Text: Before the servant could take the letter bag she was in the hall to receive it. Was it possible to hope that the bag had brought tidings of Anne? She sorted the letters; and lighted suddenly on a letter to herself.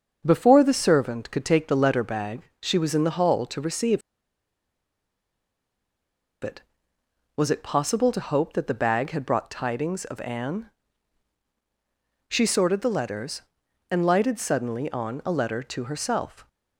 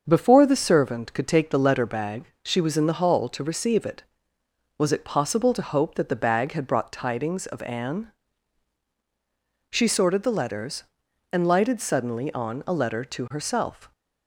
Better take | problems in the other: second | starts louder than the rest; until 1.2 s; 7 dB; also in the second // pauses between "bag" and "she"; slight; at 2.4 s; 0.18 s long; slight in the second // pauses between "receive" and "it"; strong; at 4.0 s; 2.4 s long

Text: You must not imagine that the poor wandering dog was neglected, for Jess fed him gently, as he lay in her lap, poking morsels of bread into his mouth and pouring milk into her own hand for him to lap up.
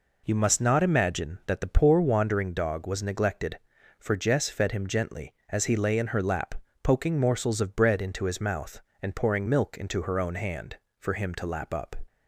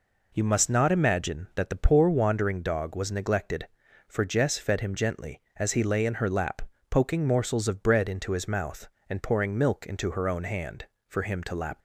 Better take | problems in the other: first | stops before "up"; at 11.7 s

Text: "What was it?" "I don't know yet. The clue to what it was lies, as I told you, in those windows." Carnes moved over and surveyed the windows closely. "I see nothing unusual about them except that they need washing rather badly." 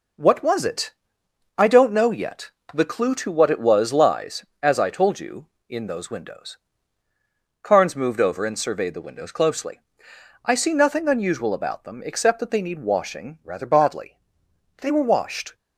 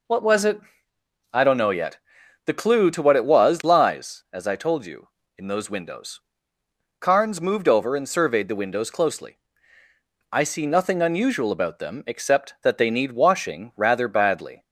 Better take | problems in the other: second | goes on to say "They were washed"; noticeable; from 14.8 s on; 0.72 s long

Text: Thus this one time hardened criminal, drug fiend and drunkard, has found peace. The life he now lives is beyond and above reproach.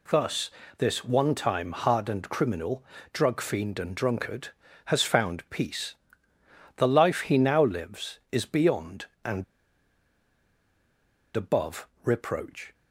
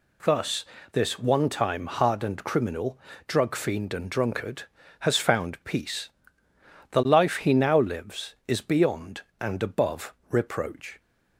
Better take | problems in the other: second | pauses between "Thus" and "this"; slight; at 0.5 s; 0.26 s long; slight in the second // pauses between "and" and "above"; strong; at 9.4 s; 1.9 s long // pauses between "above" and "reproach"; slight; at 11.8 s; 0.16 s long; slight in the second

